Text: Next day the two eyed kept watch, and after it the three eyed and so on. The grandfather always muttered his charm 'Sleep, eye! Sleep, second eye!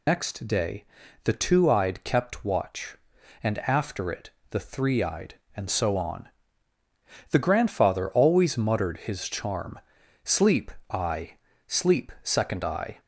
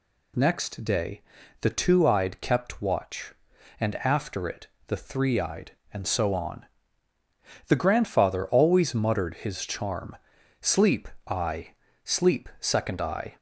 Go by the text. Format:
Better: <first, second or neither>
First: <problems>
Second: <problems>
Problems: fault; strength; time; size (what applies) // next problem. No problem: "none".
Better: second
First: loses the start of "Next"; at 0.0 s; 105 ms // pauses between "day" and "the"; at 0.8 s; 0.40 s long // pauses between "it" and "the"; slight; at 4.2 s; 0.22 s long // pauses between "charm" and "Sleep"; at 9.7 s; 0.44 s long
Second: pauses between "day" and "the"; at 1.2 s; 0.40 s long // pauses between "it" and "the"; slight; at 4.6 s; 0.22 s long // pauses between "charm" and "Sleep"; at 10.1 s; 0.44 s long